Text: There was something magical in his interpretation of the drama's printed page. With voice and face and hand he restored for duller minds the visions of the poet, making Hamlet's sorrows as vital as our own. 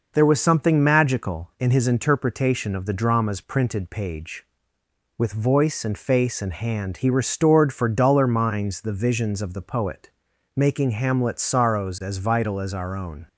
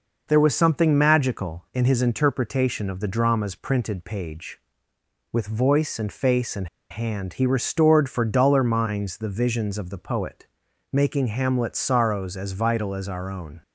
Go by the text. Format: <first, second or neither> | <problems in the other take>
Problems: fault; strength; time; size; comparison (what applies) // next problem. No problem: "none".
first | pauses between "and" and "hand"; slight; at 6.6 s; 0.24 s long